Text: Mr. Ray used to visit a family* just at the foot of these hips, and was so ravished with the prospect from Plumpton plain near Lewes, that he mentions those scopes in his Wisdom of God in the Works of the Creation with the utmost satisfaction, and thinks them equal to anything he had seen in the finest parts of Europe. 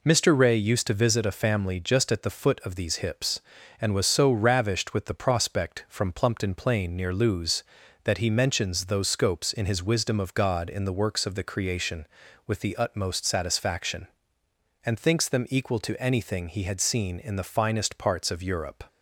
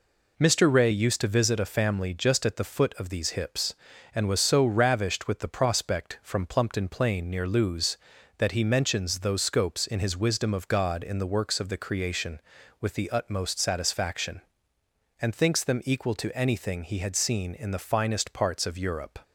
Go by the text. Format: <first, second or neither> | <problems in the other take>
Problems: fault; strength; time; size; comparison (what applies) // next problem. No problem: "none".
neither | none